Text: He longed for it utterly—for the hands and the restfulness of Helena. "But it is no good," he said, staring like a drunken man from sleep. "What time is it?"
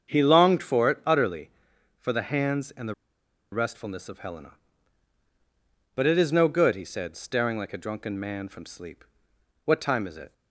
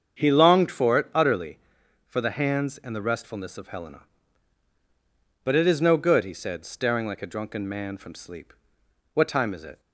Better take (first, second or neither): second